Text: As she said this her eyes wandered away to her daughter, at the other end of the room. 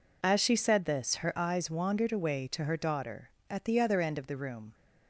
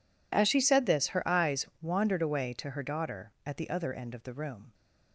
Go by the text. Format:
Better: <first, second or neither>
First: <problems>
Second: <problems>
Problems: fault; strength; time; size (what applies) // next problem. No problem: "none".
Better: neither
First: none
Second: none